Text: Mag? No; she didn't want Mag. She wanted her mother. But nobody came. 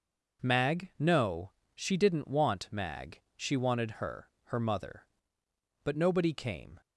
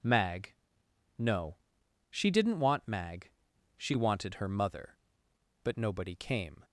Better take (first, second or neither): second